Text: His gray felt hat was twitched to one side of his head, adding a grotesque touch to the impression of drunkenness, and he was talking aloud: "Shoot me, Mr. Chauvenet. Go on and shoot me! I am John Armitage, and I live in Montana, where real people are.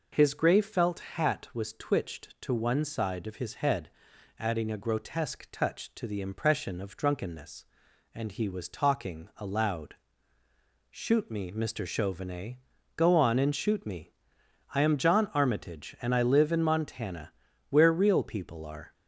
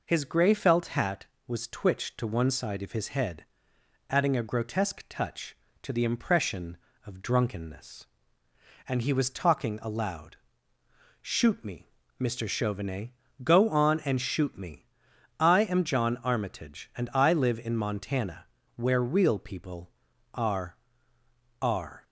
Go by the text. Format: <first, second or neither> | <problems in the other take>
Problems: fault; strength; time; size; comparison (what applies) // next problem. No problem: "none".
first | says "are" twice; at 21.6 s